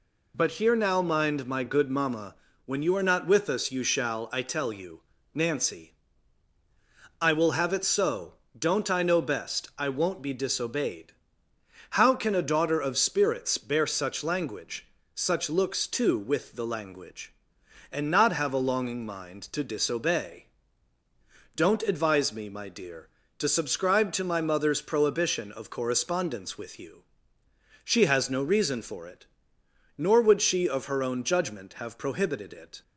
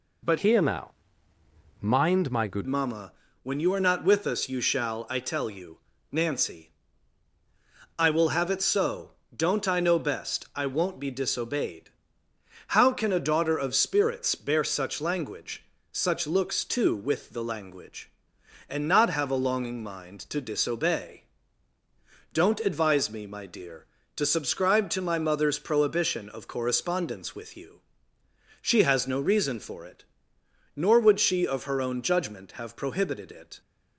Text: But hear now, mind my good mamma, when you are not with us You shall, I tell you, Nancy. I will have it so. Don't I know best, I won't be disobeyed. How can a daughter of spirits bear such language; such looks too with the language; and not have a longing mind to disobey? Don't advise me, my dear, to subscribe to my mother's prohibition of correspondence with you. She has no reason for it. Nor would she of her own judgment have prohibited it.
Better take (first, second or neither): first